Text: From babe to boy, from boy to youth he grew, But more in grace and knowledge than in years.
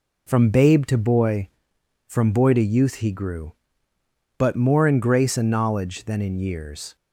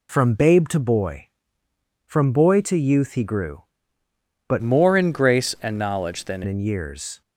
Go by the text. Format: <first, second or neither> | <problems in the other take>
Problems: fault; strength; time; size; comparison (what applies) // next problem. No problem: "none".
first | changes voice from "more" to "than"; from 4.6 to 6.4 s; 1.8 s long